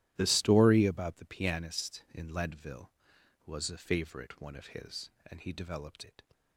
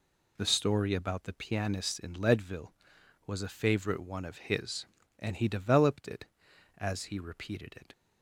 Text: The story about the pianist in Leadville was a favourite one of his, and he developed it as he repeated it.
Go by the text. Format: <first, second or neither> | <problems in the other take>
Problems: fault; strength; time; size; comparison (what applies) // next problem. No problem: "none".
second | starts louder than the rest; strong; until 1.1 s; 13.5 dB // skips "it as he repeated"; at 6.0 s